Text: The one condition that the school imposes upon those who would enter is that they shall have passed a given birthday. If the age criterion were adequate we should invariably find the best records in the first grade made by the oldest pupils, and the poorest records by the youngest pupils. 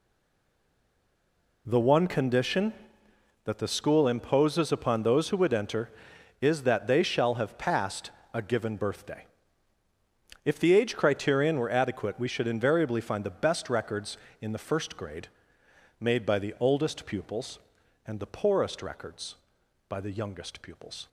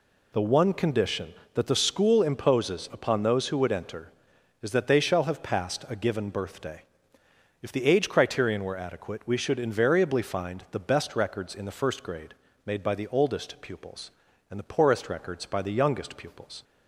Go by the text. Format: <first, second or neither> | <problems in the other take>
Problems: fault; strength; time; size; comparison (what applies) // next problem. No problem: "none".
second | stays silent before the first word; noticeable; until 1.6 s; 1.6 s long // pauses between "passed" and "a"; slight; at 8.1 s; 0.20 s long // pauses between "grade" and "made"; noticeable; at 15.2 s; 0.72 s long; slight in the second